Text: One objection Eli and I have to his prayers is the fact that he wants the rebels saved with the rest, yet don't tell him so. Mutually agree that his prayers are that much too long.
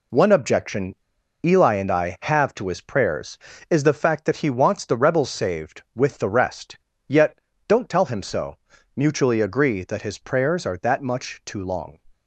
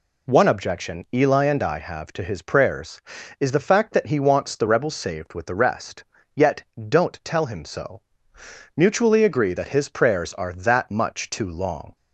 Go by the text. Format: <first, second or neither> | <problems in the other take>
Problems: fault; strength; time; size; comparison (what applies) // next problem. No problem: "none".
second | pauses between "objection" and "Eli"; noticeable; at 0.9 s; 0.49 s long // pauses between "yet" and "don't"; slight; at 7.3 s; 0.30 s long; slight in the second